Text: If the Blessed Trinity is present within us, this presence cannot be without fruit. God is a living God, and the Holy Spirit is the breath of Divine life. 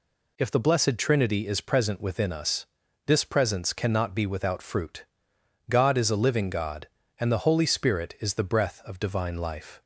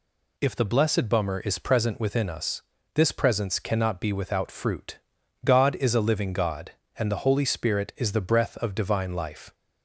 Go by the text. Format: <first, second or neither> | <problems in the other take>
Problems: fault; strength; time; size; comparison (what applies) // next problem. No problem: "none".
first | says "Bummer" for "Trinity"; at 1.0 s